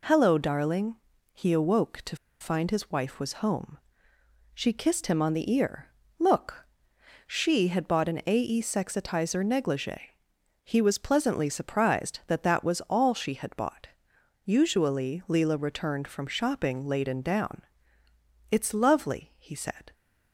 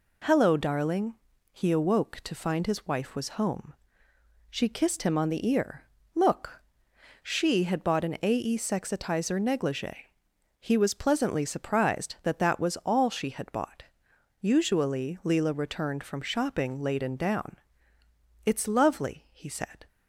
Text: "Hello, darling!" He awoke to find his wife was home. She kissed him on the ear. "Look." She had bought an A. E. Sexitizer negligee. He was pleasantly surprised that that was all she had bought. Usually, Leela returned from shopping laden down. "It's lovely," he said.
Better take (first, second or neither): second